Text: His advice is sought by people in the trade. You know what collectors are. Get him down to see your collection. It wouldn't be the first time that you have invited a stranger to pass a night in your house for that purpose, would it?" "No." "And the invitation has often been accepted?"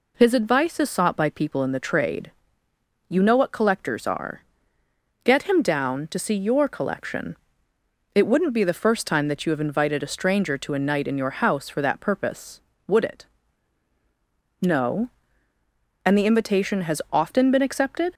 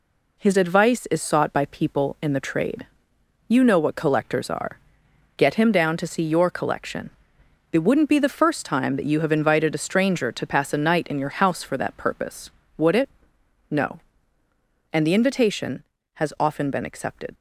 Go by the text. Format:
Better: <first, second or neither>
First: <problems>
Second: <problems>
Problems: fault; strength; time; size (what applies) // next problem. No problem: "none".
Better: second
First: skips "pass"; at 10.7 s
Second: none